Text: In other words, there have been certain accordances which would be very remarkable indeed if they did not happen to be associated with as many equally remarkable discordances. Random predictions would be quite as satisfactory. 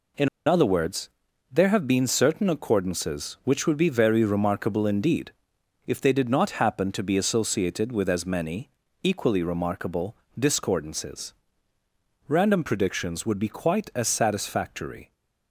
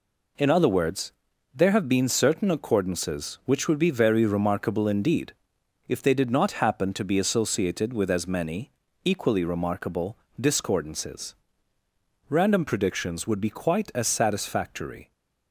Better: second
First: pauses between "In" and "other"; slight; at 0.2 s; 0.17 s long // pauses between "indeed" and "if"; noticeable; at 5.3 s; 0.54 s long // pauses between "many" and "equally"; slight; at 8.7 s; 0.32 s long // pauses between "remarkable" and "discordances"; slight; at 10.1 s; 0.24 s long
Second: pauses between "indeed" and "if"; noticeable; at 5.3 s; 0.54 s long // pauses between "many" and "equally"; slight; at 8.7 s; 0.32 s long // pauses between "remarkable" and "discordances"; slight; at 10.1 s; 0.24 s long

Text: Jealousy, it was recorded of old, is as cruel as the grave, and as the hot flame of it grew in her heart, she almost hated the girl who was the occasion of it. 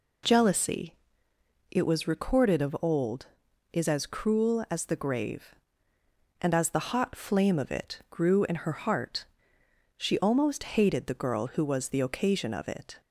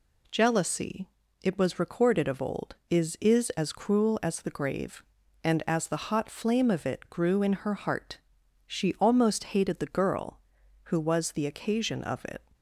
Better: first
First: none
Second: says "is" twice; at 3.1 s

